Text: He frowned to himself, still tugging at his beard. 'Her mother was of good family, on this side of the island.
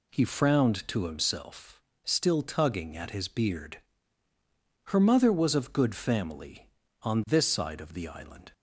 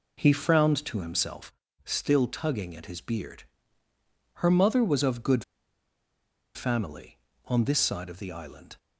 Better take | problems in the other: first | pauses between "good" and "family"; at 5.4 s; 1.1 s long

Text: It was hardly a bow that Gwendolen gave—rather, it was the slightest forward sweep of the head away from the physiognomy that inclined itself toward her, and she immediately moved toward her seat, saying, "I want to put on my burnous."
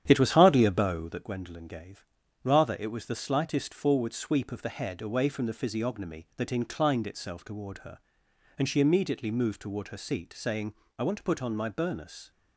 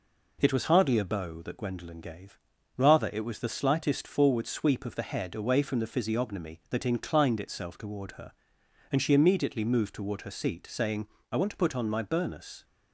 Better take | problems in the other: second | starts louder than the rest; strong; until 1.3 s; 10 dB

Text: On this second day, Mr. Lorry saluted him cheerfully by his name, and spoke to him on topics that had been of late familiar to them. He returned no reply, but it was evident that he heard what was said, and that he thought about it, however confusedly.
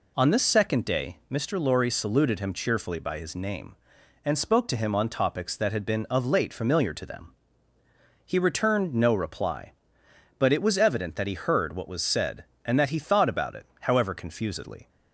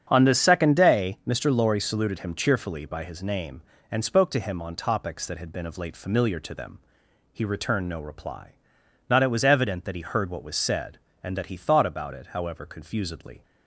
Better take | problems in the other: first | starts louder than the rest; strong; until 1.1 s; 7.5 dB // says "not" for "but"; at 9.1 s

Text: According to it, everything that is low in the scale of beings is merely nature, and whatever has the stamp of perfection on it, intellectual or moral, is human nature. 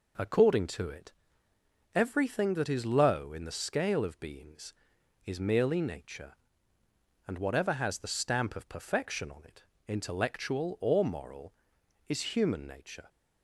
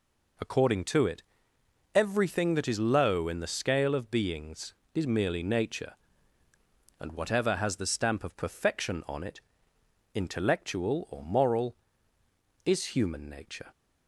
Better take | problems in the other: neither | none

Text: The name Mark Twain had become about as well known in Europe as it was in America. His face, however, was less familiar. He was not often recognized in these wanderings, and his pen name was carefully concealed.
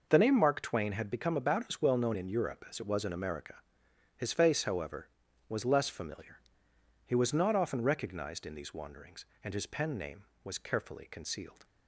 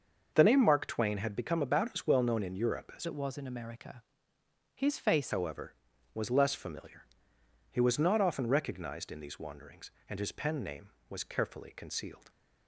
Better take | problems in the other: first | starts louder than the rest; until 1.3 s; 6.5 dB // changes voice from "it" to "face"; from 3.0 to 5.3 s; 2.3 s long

